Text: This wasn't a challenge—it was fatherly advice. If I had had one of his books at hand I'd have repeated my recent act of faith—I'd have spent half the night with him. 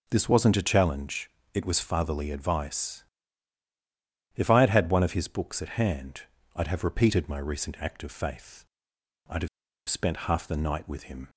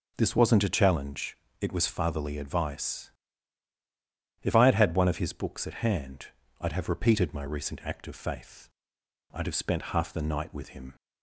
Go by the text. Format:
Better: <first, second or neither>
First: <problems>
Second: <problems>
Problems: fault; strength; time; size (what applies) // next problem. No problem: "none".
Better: second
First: pauses between "hand" and "I'd"; slight; at 6.2 s; 0.34 s long // pauses between "have" and "spent"; at 9.4 s; 0.41 s long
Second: pauses between "hand" and "I'd"; slight; at 6.2 s; 0.34 s long